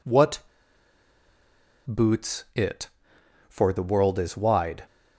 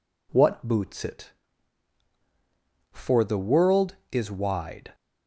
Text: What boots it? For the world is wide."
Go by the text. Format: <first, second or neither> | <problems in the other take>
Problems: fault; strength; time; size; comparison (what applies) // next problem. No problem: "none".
second | pauses between "What" and "boots"; strong; at 0.4 s; 1.4 s long